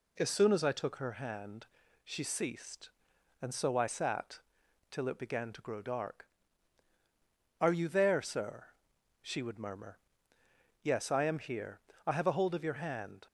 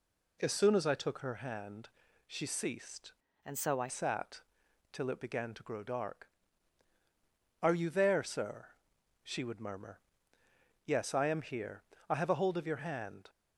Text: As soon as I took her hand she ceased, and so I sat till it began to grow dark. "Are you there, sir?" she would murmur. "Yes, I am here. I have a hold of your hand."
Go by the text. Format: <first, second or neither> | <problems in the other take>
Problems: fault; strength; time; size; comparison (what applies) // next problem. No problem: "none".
first | pauses between "hand" and "she"; at 1.8 s; 0.40 s long; also in the first // changes voice from "and" to "I"; from 3.4 to 3.8 s; 0.4 s long // pauses between "sat" and "till"; noticeable; at 4.3 s; 0.54 s long; noticeable in the first